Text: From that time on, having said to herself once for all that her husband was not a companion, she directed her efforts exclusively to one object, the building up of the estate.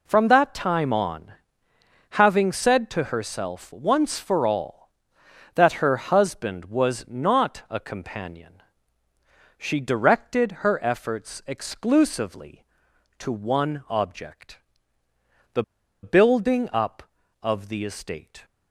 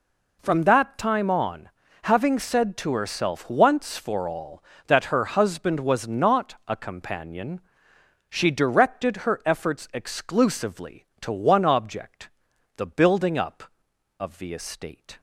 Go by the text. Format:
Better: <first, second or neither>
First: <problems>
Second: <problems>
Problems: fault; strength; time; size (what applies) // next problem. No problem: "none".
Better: second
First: pauses between "the" and "building"; at 15.6 s; 0.38 s long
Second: none